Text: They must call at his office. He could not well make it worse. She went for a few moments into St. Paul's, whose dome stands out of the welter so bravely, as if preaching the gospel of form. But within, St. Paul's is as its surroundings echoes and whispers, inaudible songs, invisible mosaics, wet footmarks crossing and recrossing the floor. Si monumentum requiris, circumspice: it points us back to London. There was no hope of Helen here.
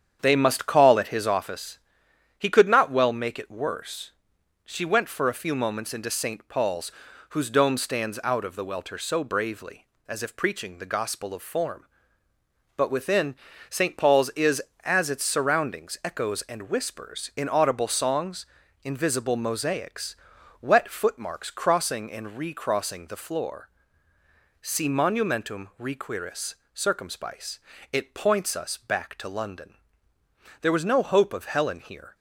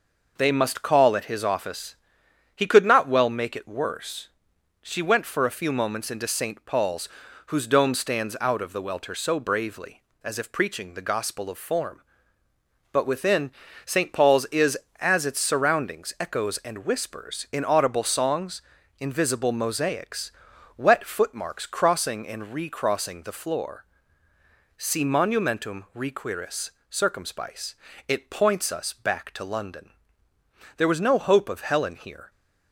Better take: second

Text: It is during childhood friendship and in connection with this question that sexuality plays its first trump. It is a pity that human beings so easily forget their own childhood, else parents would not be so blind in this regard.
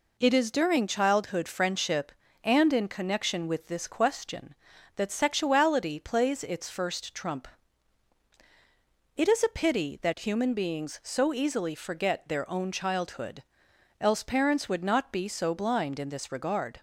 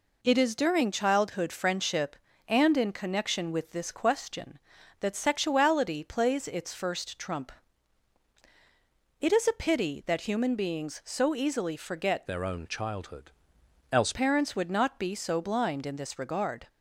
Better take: first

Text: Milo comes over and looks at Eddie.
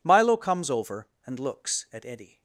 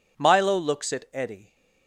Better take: first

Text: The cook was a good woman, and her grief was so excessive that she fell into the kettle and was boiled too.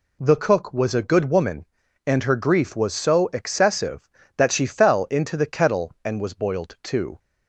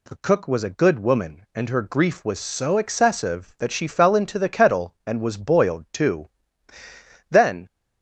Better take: first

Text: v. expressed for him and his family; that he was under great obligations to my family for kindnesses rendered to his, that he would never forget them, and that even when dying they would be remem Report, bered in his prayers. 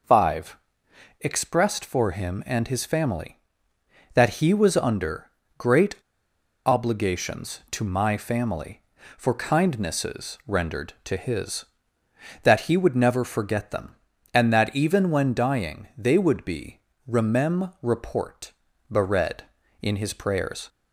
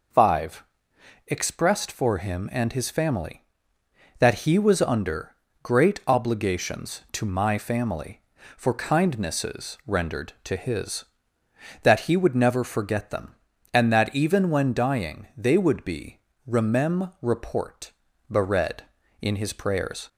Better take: second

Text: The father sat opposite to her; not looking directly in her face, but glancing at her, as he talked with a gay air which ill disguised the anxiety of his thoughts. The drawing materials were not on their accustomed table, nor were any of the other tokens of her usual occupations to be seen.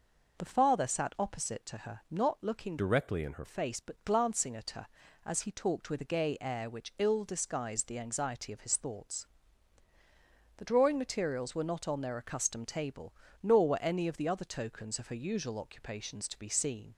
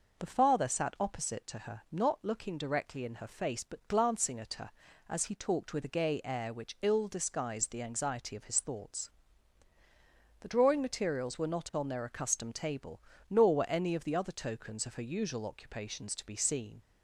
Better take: second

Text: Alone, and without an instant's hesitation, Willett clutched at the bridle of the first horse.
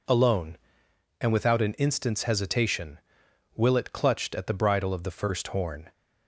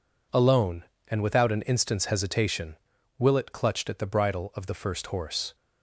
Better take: second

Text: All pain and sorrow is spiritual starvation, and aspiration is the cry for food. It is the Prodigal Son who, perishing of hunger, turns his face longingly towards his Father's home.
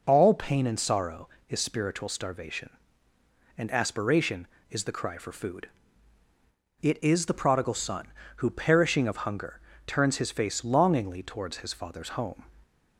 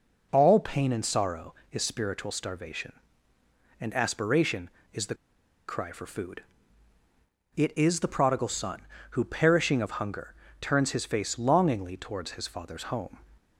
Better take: first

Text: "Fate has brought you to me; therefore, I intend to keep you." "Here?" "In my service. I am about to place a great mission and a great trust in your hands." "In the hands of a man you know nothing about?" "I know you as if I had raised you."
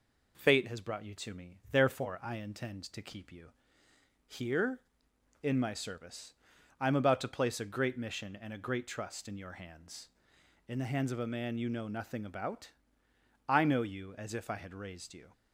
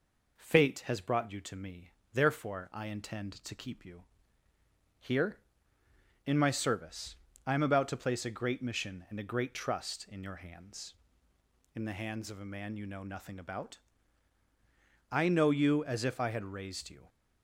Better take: neither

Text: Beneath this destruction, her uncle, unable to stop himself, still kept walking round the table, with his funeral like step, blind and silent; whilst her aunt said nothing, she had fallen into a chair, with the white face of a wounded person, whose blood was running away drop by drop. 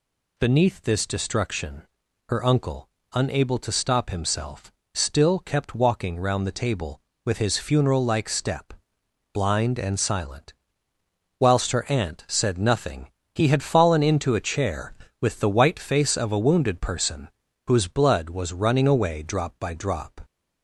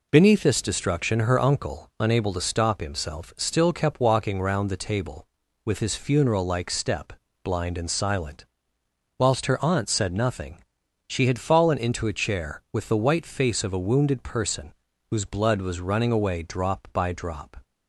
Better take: second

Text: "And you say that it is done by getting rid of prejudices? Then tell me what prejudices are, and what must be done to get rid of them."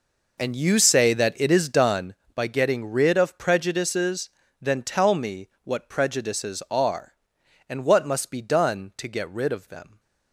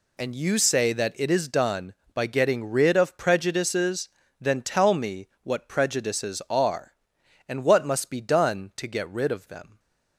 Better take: second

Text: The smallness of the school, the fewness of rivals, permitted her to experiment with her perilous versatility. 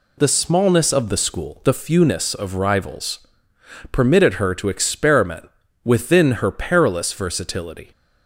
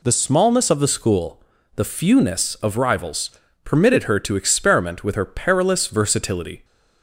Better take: second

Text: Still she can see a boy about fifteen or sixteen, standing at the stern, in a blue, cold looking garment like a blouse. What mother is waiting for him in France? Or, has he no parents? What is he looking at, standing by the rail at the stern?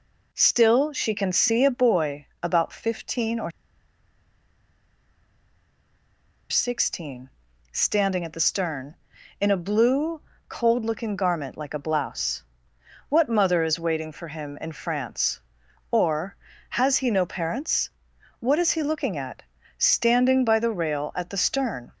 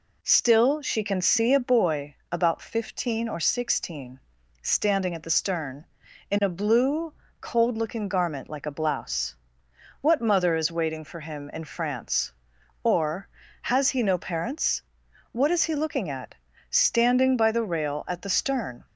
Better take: second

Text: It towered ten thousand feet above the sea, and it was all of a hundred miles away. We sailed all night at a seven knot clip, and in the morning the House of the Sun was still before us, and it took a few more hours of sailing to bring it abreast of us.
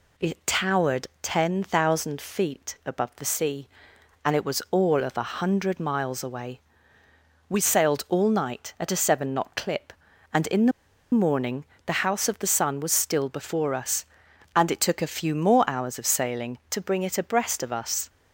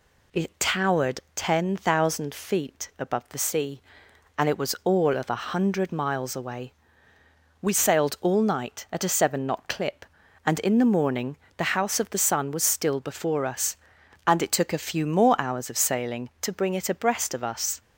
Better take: second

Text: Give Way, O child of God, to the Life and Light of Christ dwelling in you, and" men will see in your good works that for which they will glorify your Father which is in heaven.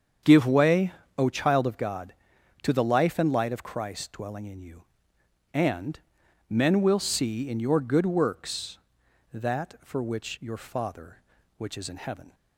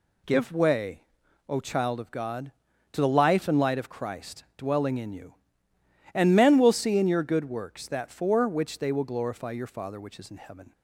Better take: second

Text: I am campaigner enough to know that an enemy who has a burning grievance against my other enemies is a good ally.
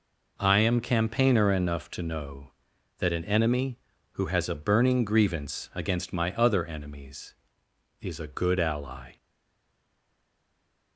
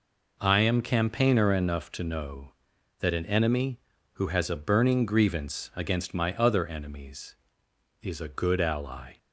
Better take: second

